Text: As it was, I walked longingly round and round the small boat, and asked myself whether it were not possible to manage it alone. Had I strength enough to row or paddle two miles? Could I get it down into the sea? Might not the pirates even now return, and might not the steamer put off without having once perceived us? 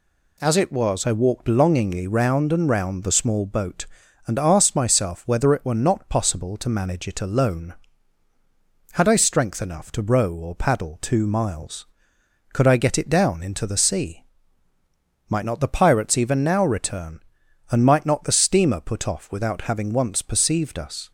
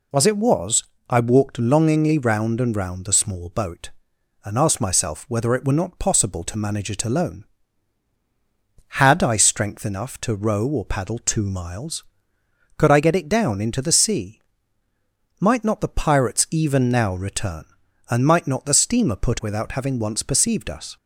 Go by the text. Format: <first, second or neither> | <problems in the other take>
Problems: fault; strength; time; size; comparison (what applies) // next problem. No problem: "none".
first | skips "off"; at 19.3 s